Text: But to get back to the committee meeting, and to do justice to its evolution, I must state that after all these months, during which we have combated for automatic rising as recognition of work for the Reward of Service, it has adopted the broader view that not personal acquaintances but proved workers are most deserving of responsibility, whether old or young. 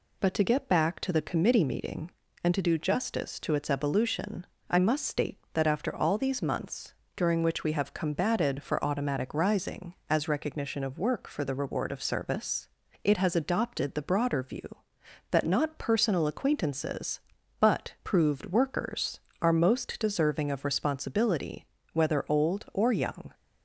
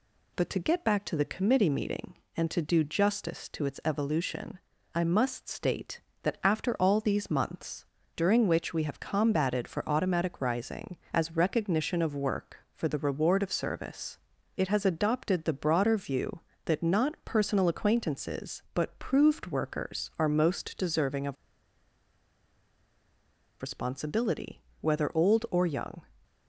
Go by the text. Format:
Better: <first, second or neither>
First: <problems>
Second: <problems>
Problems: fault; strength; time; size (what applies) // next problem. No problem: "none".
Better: first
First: none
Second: pauses between "of" and "responsibility"; strong; at 21.3 s; 2.2 s long